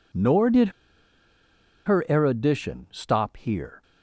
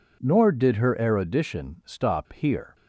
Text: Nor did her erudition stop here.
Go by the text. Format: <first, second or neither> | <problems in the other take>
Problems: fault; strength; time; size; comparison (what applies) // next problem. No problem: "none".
second | pauses between "did" and "her"; at 0.6 s; 1.1 s long